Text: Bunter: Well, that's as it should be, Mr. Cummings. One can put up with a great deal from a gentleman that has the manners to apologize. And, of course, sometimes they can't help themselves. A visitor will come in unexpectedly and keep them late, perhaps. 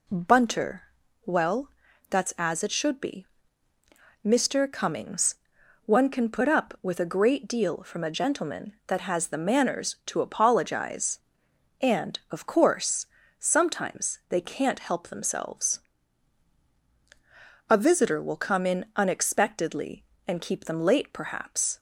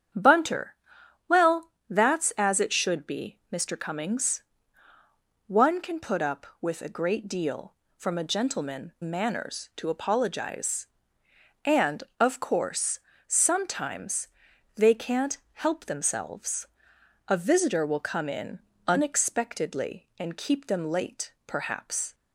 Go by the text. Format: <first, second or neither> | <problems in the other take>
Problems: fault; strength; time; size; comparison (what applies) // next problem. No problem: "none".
first | starts louder than the rest; strong; until 1.6 s; 8.5 dB // skips "that has the"; at 8.9 s // pauses between "sometimes" and "they"; noticeable; at 14.2 s; 0.48 s long // pauses between "can't" and "help"; slight; at 15.3 s; 0.16 s long // pauses between "in" and "unexpectedly"; slight; at 18.6 s; 0.28 s long